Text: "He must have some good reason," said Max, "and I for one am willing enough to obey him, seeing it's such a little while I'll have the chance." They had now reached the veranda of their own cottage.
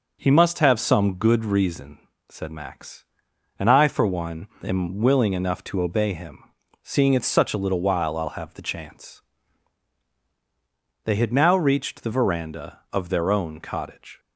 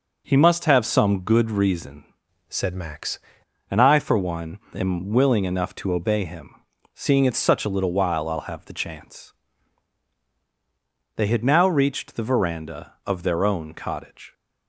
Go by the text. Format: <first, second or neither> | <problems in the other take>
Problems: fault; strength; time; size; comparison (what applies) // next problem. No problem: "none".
first | changes voice from "said" to "Max"; from 2.4 to 3.1 s; 0.7 s long